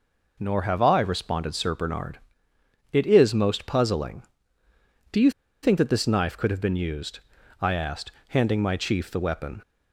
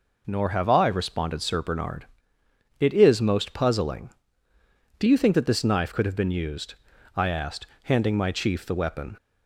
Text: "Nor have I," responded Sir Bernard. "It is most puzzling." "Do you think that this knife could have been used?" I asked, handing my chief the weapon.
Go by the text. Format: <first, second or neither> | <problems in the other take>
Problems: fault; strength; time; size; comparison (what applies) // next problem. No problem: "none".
second | pauses between "you" and "think"; slight; at 5.3 s; 0.32 s long